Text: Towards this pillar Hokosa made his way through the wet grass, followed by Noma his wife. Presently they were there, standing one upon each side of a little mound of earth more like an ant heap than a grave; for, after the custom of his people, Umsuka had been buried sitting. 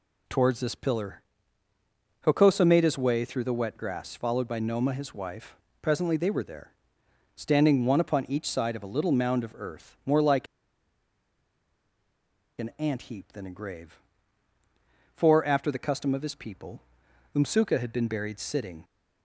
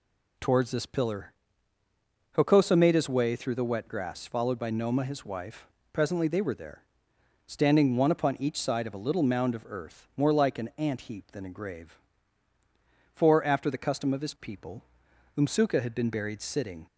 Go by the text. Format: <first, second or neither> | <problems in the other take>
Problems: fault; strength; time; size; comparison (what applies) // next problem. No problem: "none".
second | pauses between "pillar" and "Hokosa"; at 1.2 s; 1.0 s long; also in the second // pauses between "like" and "an"; strong; at 10.4 s; 2.1 s long